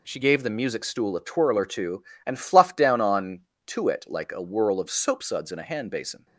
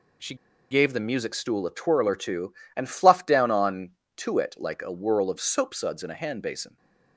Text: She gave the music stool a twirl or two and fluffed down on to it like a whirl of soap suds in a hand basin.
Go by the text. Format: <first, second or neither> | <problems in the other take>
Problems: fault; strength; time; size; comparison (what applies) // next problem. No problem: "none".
first | pauses between "She" and "gave"; slight; at 0.3 s; 0.36 s long